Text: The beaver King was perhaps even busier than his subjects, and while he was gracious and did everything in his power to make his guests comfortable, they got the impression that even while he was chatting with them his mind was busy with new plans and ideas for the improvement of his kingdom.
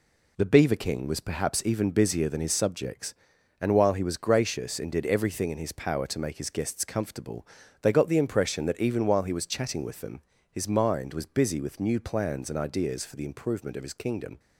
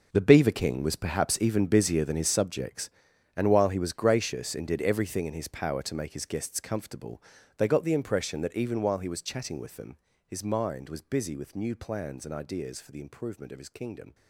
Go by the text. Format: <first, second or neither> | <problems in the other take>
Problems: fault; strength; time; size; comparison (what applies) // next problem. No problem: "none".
first | gets quieter; strong; throughout; 14.5 dB // pauses between "them" and "his"; slight; at 9.9 s; 0.30 s long; slight in the first